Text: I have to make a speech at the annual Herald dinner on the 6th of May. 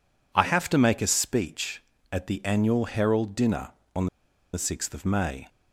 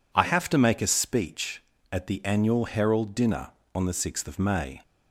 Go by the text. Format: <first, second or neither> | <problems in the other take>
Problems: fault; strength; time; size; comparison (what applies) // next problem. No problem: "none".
second | pauses between "on" and "the"; noticeable; at 4.0 s; 0.47 s long